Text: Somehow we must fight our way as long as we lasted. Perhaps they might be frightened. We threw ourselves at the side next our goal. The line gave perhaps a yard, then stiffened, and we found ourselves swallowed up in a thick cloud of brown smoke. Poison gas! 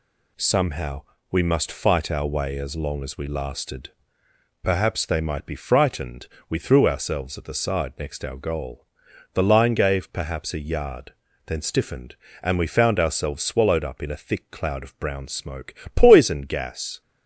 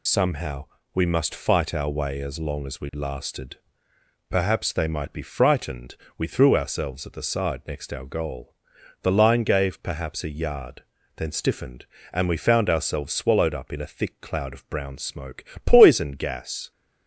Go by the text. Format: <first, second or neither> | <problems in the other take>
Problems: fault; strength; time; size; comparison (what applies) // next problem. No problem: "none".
first | loses the start of "Somehow"; at 0.0 s; 65 ms // pauses between "Somehow" and "we"; slight; at 0.6 s; 0.28 s long; slight in the first